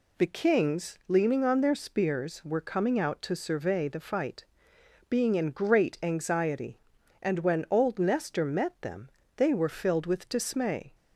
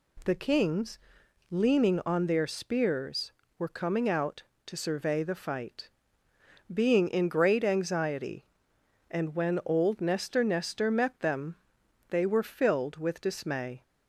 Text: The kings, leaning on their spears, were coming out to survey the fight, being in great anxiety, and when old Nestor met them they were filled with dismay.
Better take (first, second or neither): first